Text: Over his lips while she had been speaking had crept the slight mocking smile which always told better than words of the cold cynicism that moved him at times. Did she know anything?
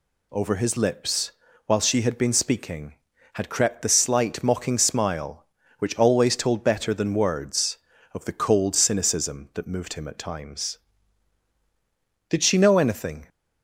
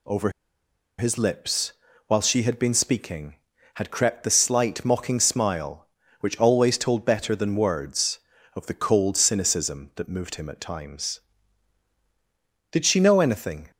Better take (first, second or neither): first